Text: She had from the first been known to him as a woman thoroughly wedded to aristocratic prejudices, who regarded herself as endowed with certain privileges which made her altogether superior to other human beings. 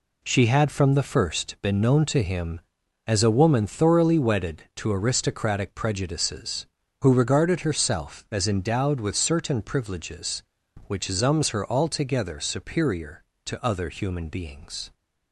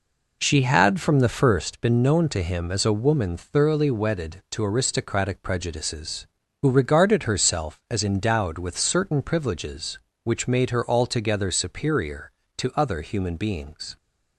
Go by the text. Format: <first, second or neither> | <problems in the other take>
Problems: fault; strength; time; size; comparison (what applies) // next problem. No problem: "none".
second | says "zums" for "made"; at 11.0 s